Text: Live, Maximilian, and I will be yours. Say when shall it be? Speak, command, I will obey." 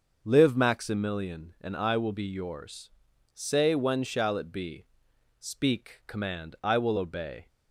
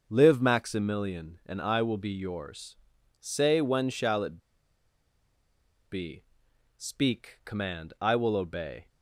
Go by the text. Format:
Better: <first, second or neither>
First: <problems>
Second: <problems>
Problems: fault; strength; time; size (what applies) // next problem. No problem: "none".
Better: first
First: starts louder than the rest; noticeable; until 1.2 s; 6 dB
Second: starts louder than the rest; noticeable; until 1.0 s; 6 dB // pauses between "it" and "be"; strong; at 4.3 s; 1.5 s long